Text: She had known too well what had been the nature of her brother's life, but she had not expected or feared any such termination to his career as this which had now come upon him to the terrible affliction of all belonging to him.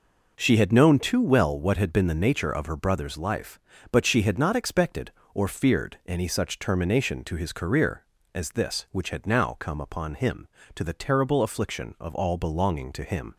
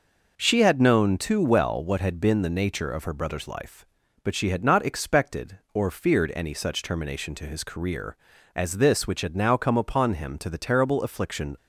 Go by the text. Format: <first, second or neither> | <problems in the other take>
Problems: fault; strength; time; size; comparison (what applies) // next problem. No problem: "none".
first | stops before "of all belonging to him"; at 11.5 s